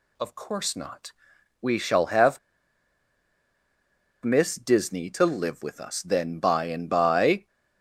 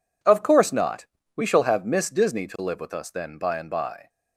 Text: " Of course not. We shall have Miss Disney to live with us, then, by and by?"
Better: second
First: pauses between "have" and "Miss"; strong; at 2.3 s; 1.8 s long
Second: none

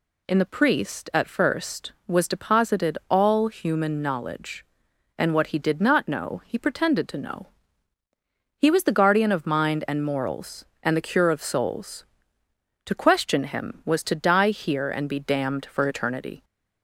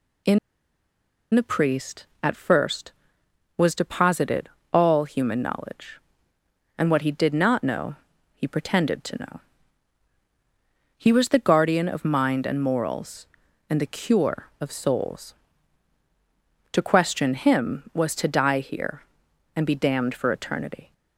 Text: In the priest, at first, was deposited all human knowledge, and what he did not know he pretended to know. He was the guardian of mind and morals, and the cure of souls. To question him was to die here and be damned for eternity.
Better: first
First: none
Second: pauses between "In" and "the"; noticeable; at 0.3 s; 0.96 s long // pauses between "deposited" and "all"; slight; at 4.4 s; 0.24 s long // pauses between "know" and "he"; at 7.9 s; 0.38 s long

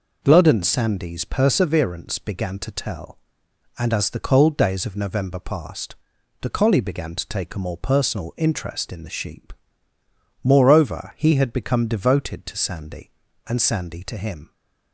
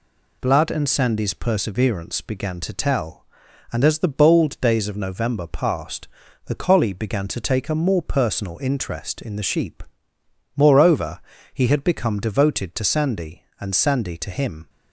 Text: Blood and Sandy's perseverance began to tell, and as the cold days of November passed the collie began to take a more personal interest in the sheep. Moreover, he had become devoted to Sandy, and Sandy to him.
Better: first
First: pauses between "passed" and "the"; noticeable; at 5.9 s; 0.46 s long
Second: says "bold" for "cold"; at 4.0 s // pauses between "passed" and "the"; at 6.0 s; 0.38 s long

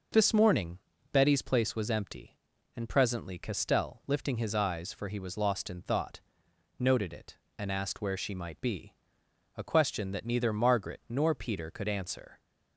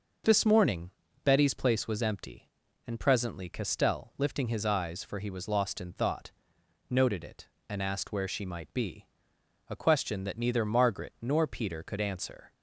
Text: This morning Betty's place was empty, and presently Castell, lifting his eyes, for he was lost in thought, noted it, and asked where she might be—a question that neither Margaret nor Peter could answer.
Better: neither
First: pauses between "morning" and "Betty's"; slight; at 0.7 s; 0.34 s long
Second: pauses between "morning" and "Betty's"; slight; at 0.8 s; 0.34 s long

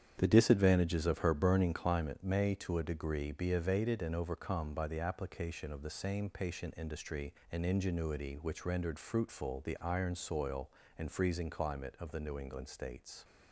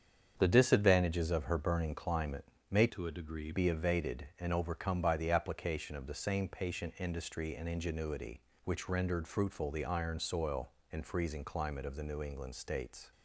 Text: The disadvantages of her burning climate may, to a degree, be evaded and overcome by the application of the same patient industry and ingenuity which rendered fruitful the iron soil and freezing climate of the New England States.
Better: first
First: starts louder than the rest; strong; until 1.1 s; 9 dB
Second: starts louder than the rest; strong; until 1.3 s; 7.5 dB // pauses between "climate" and "may"; slight; at 2.4 s; 0.24 s long // changes voice from "to" to "degree"; from 2.9 to 3.5 s; 0.6 s long

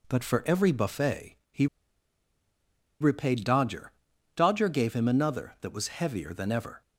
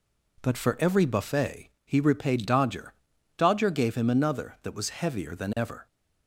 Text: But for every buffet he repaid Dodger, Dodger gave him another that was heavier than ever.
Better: second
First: pauses between "buffet" and "he"; slight; at 1.3 s; 0.16 s long // pauses between "he" and "repaid"; strong; at 1.6 s; 1.3 s long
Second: pauses between "buffet" and "he"; slight; at 1.6 s; 0.16 s long

